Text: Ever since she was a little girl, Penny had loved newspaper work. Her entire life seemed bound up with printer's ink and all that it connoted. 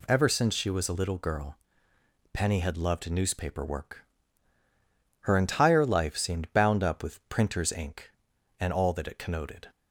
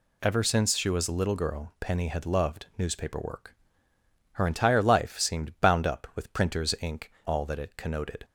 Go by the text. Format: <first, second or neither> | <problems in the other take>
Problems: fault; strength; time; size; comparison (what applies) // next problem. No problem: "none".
first | skips "and"; at 7.1 s